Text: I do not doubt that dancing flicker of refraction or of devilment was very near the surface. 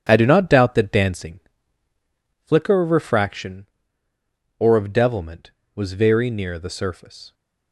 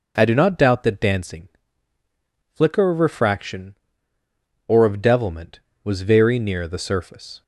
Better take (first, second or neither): second